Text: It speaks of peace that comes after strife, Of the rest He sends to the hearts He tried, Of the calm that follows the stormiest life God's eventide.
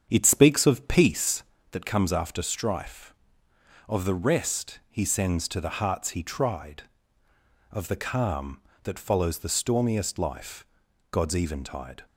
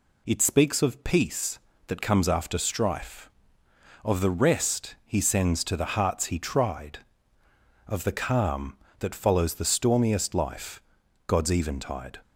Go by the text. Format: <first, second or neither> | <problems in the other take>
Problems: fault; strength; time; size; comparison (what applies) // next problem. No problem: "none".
second | starts louder than the rest; strong; until 1.5 s; 8 dB // pauses between "life" and "God's"; noticeable; at 10.6 s; 0.46 s long; noticeable in the second